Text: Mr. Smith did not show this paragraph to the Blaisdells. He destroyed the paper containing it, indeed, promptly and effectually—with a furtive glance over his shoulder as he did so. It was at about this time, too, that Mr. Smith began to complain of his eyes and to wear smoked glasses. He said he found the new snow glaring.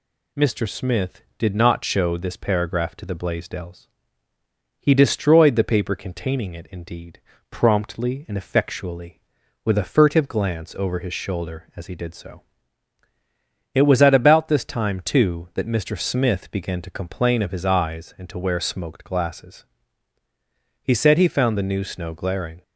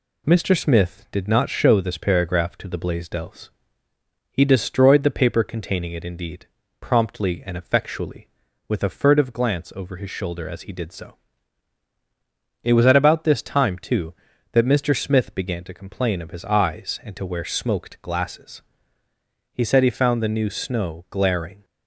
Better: neither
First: none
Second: none

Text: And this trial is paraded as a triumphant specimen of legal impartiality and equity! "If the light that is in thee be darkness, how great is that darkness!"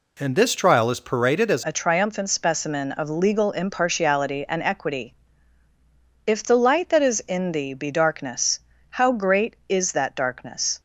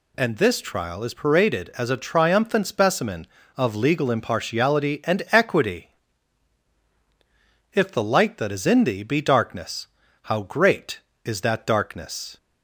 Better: second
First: changes voice at "a"; from 1.6 s on; 9.2 s long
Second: none

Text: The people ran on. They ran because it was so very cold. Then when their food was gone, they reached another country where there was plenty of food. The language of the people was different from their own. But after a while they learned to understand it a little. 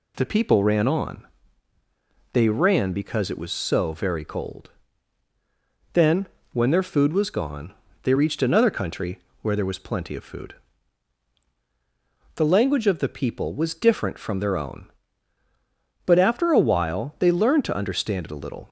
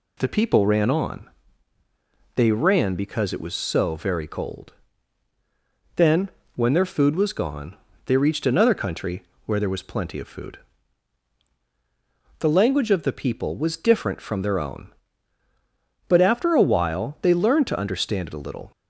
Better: neither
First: pauses between "Then" and "when"; slight; at 6.2 s; 0.28 s long // pauses between "country" and "where"; slight; at 9.1 s; 0.24 s long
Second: pauses between "Then" and "when"; slight; at 6.2 s; 0.28 s long // pauses between "country" and "where"; slight; at 9.2 s; 0.24 s long

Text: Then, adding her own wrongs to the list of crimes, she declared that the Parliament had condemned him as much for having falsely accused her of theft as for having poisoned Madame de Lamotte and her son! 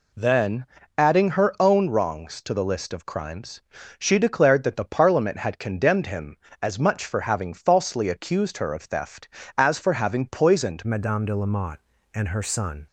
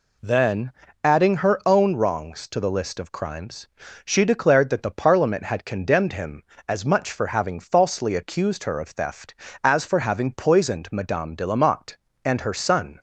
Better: second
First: changes voice at "Madame"; from 10.8 s on; 2.0 s long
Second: none

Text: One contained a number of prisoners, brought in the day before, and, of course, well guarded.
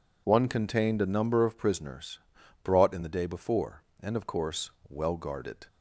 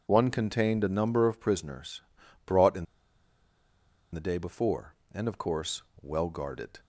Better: first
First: none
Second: pauses between "in" and "the"; strong; at 2.8 s; 1.2 s long

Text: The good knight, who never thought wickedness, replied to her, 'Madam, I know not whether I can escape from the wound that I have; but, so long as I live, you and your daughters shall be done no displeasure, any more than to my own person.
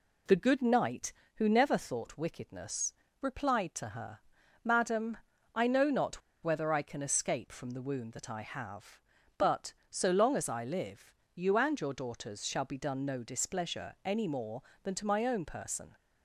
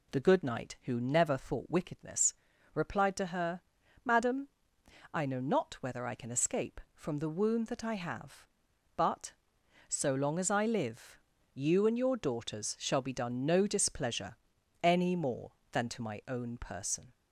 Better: second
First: pauses between "not" and "whether"; slight; at 6.2 s; 0.22 s long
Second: none

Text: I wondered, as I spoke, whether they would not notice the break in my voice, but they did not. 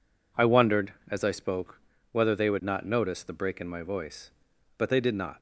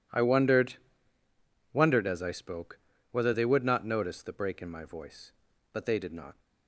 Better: first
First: none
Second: says "wondered" twice; at 1.7 s

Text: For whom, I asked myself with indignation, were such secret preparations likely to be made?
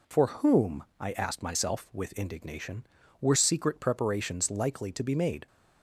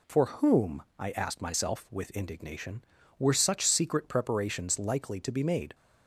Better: second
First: skips "such"; at 3.3 s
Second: none

